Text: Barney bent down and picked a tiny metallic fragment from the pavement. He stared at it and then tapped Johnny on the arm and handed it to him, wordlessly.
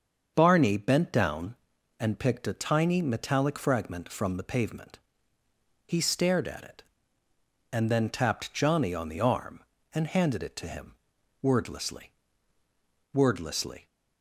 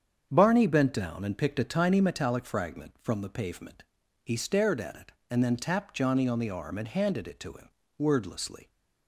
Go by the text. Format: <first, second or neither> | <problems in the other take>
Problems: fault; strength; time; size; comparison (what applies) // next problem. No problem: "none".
second | starts louder than the rest; until 1.3 s; 7 dB; strong in the second // says "wordlessly" twice; at 13.1 s